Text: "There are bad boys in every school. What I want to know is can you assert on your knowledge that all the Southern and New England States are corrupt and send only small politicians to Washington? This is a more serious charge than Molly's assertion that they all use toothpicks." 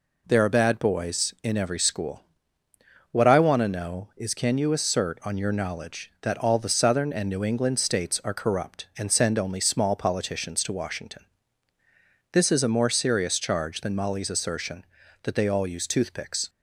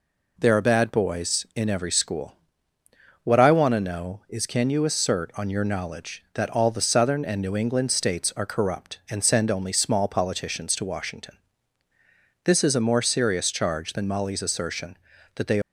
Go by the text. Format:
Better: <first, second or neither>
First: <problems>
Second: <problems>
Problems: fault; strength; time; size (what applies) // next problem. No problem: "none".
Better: first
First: none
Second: stops before "all use toothpicks"; at 15.6 s